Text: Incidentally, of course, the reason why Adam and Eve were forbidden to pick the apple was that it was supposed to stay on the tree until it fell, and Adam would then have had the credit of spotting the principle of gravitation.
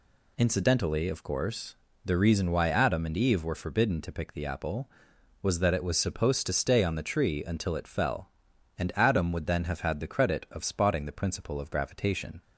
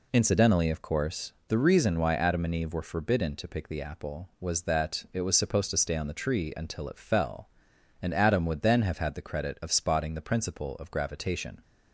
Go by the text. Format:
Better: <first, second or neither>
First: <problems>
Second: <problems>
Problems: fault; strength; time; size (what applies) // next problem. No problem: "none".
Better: neither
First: none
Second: none